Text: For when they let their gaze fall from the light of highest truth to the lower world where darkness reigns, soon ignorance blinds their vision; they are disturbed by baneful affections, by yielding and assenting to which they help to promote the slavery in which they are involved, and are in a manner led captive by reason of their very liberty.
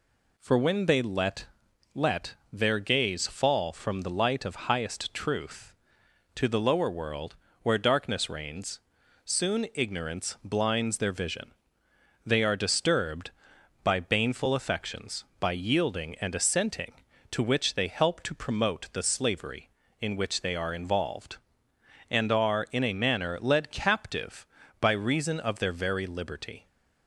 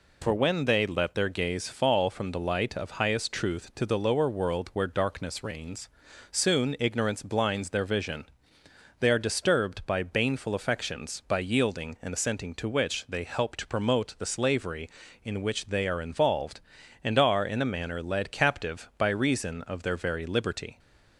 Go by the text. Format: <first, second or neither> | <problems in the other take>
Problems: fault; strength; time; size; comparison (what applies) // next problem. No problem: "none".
second | says "let" twice; at 1.9 s // pauses between "world" and "where"; slight; at 7.3 s; 0.28 s long